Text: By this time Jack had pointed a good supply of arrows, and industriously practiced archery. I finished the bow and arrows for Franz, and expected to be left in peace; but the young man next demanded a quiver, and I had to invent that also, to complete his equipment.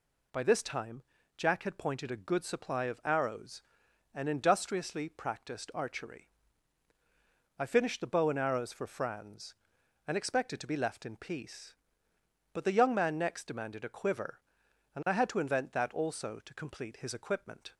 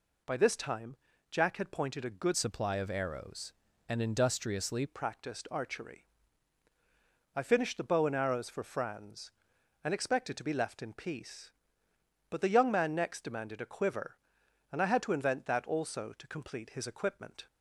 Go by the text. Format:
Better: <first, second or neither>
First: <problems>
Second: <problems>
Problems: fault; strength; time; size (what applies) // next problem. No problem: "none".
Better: first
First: pauses between "time" and "Jack"; slight; at 1.0 s; 0.34 s long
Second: pauses between "time" and "Jack"; slight; at 0.9 s; 0.34 s long // changes voice from "supply" to "industriously"; from 2.3 to 4.8 s; 2.5 s long